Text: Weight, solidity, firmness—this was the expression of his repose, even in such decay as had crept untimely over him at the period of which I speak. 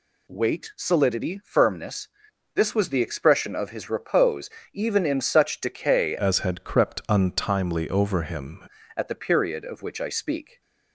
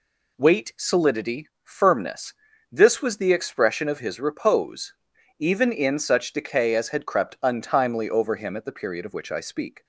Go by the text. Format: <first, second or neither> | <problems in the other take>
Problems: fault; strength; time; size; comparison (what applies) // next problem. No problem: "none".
second | changes voice from "as" to "him"; from 6.1 to 8.6 s; 2.5 s long